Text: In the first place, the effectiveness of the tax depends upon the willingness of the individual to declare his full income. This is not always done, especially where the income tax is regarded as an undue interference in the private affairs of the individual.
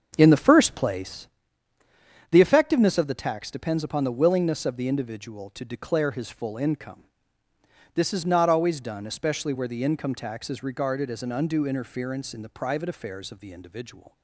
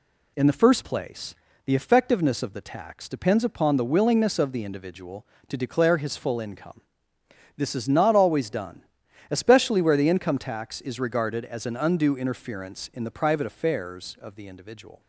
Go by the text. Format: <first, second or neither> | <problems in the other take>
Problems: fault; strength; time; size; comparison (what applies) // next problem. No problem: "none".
second | starts louder than the rest; until 1.3 s; 7 dB